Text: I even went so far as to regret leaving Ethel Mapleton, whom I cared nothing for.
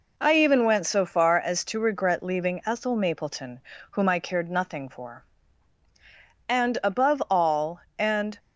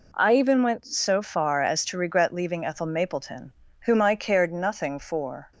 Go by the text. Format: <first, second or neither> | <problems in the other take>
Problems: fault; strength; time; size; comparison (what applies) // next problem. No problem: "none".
second | goes on to say "And above all and"; strong; from 6.4 s on; 1.9 s long